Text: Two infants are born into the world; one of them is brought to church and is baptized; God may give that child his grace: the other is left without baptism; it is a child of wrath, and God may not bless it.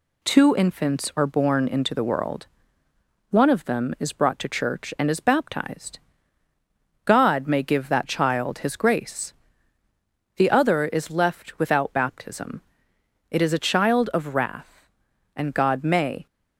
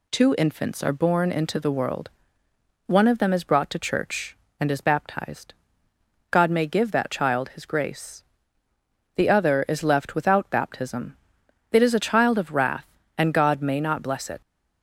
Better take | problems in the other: second | stops before "not bless it"; at 16.2 s

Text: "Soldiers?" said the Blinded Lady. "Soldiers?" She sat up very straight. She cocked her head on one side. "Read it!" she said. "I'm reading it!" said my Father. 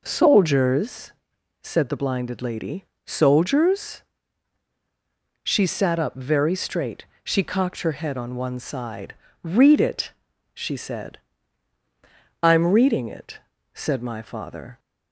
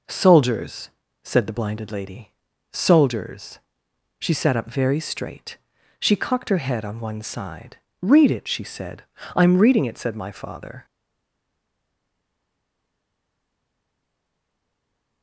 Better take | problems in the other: first | stays silent after the last word; strong; from 10.8 s on; 4.4 s long

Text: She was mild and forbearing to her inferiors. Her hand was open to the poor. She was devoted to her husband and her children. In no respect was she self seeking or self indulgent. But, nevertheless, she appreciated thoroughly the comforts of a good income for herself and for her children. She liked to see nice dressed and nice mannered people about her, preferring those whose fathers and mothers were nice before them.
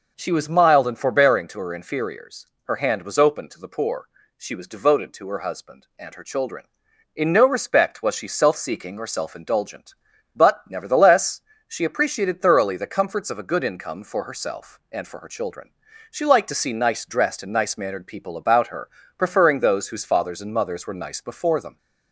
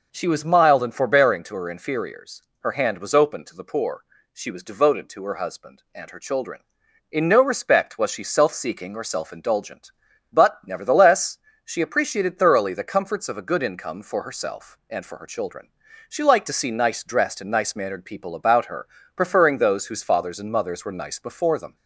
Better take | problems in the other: neither | none

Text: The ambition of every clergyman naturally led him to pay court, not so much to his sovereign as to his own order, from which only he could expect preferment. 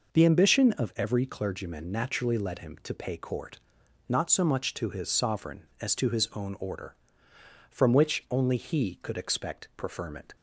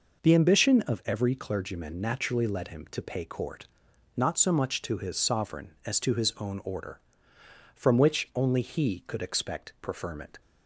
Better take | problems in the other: neither | none

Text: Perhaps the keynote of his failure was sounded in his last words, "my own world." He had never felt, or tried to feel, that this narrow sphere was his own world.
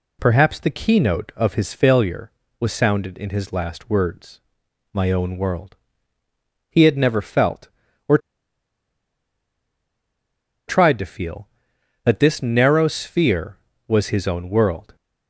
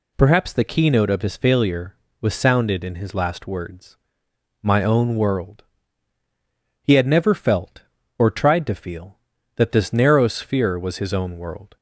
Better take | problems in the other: second | pauses between "or" and "tried"; strong; at 8.1 s; 2.4 s long

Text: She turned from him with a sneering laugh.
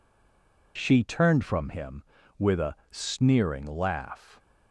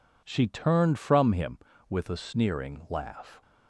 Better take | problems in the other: second | stays silent before the first word; slight; until 0.7 s; 0.7 s long // pauses between "a" and "sneering"; slight; at 2.7 s; 0.16 s long

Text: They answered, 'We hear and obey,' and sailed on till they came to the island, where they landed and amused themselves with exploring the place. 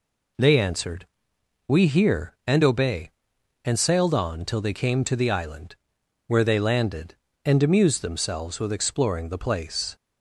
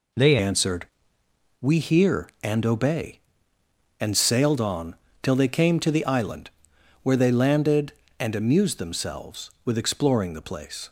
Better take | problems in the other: first | changes voice at "answered"; from 0.4 s on; 10.4 s long // pauses between "on" and "till"; slight; at 4.9 s; 0.26 s long

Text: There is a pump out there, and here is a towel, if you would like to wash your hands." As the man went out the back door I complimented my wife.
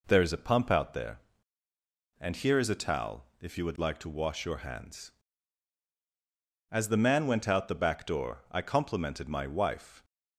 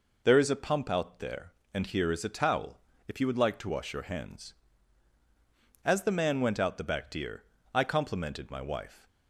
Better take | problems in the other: first | says "deer" for "door"; at 7.1 s

